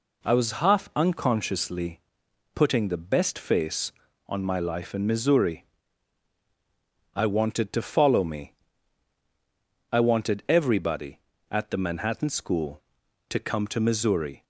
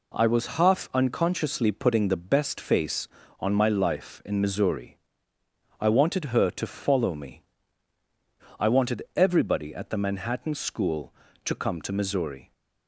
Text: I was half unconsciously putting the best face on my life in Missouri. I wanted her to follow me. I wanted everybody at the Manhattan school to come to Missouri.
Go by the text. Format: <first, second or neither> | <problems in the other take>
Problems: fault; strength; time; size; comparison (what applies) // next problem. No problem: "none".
second | pauses between "unconsciously" and "putting"; noticeable; at 1.9 s; 0.54 s long // skips "her"; at 7.7 s